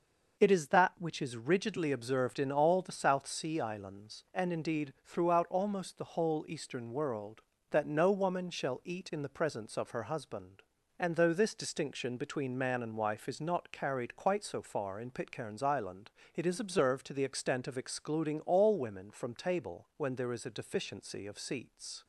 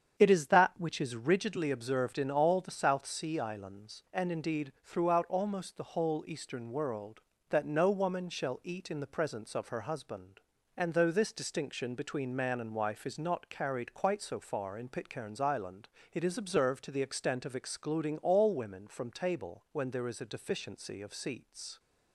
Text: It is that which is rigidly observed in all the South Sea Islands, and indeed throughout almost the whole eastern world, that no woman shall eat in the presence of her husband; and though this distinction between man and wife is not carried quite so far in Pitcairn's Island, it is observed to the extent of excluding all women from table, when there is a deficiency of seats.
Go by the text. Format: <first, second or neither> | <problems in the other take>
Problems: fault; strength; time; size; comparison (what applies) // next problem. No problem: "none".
first | starts louder than the rest; strong; until 1.6 s; 8 dB